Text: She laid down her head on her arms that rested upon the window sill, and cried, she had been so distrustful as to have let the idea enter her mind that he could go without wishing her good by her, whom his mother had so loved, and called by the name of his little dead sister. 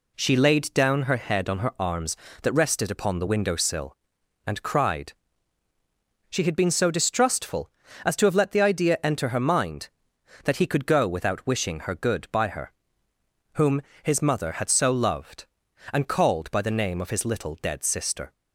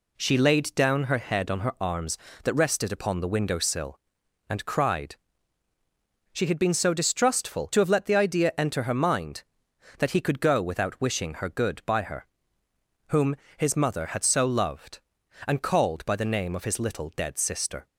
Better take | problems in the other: first | skips "as"; at 7.7 s // pauses between "whom" and "his"; slight; at 13.3 s; 0.20 s long; slight in the first

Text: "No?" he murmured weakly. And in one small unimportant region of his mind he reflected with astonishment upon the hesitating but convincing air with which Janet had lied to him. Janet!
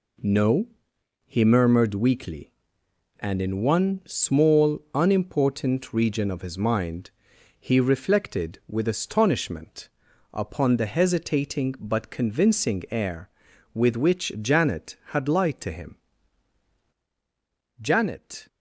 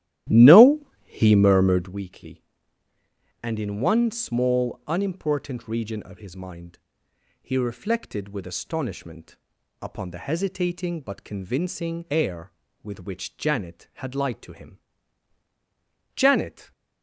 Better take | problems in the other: first | starts louder than the rest; strong; until 2.0 s; 13.5 dB // pauses between "mind" and "he"; noticeable; at 6.7 s; 0.60 s long; noticeable in the first // pauses between "astonishment" and "upon"; at 9.3 s; 0.44 s long; also in the first

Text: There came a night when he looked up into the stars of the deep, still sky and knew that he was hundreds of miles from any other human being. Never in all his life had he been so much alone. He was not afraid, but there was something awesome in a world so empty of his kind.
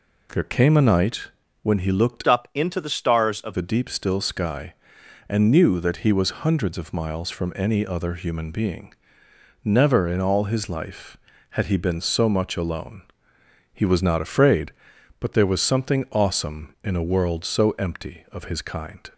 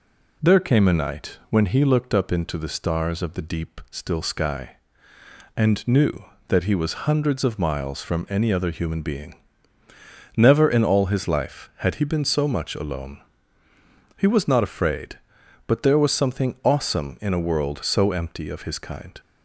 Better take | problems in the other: second | pauses between "night" and "when"; at 1.2 s; 0.38 s long // changes voice from "up" to "of"; from 2.2 to 3.5 s; 1.3 s long

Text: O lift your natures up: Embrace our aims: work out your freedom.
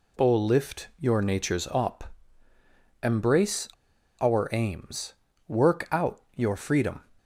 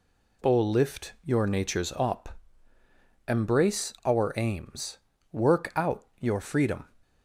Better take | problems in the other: second | pauses between "Embrace" and "our"; noticeable; at 3.6 s; 0.51 s long

